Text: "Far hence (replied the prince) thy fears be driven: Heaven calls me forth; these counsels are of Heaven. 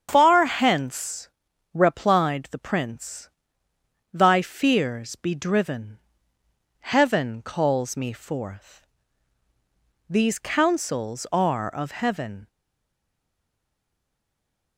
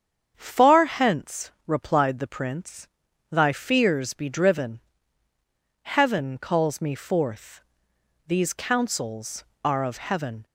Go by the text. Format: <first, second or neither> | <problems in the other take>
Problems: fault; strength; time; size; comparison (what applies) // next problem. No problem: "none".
second | starts louder than the rest; strong; until 1.1 s; 7.5 dB; strong in the second // stays silent after the last word; from 12.4 s on; 2.3 s long